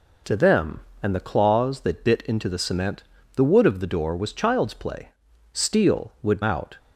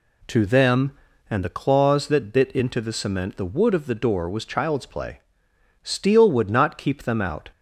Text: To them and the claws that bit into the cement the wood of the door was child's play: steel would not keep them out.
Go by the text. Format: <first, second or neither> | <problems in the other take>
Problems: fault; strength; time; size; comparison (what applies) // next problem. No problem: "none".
second | pauses between "cement" and "the"; slight; at 3.0 s; 0.32 s long // skips "not keep them"; at 6.4 s